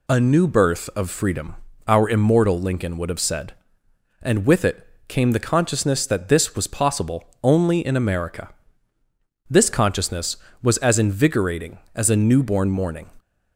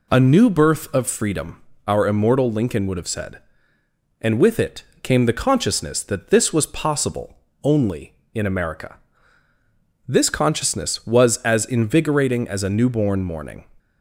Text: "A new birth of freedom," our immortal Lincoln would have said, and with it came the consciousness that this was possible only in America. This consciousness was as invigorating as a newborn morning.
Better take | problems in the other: neither | pauses between "it" and "came"; slight; the same in both // pauses between "possible" and "only"; slight; the same in both

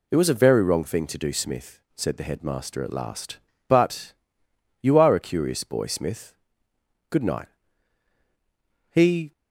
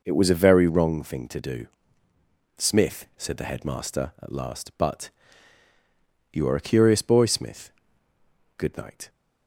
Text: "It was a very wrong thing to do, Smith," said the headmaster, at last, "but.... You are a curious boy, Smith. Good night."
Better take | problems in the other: second | goes on to say "He"; slight; from 8.9 s on; 0.40 s long

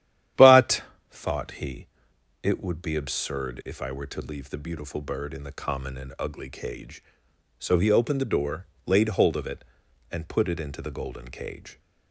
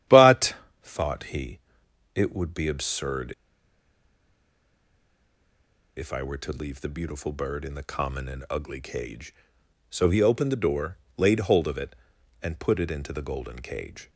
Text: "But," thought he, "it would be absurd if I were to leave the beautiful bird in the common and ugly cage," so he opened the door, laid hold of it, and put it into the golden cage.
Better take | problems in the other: first | starts louder than the rest; strong; until 1.3 s; 11 dB; strong in the first // pauses between "absurd" and "if"; strong; at 3.3 s; 2.6 s long

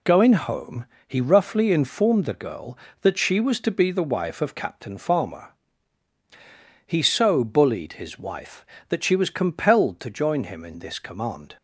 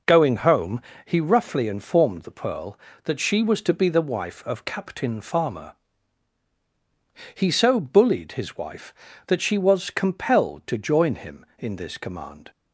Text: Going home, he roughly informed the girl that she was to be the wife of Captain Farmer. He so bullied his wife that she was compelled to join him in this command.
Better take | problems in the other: first | says "pearl" for "girl"; at 2.3 s

